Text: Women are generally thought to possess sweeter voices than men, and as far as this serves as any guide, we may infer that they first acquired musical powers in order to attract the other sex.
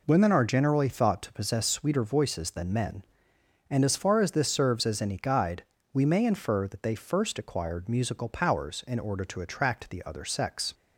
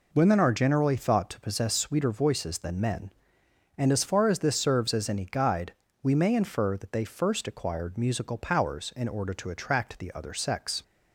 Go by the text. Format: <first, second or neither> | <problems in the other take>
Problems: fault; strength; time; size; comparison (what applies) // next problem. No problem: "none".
neither | none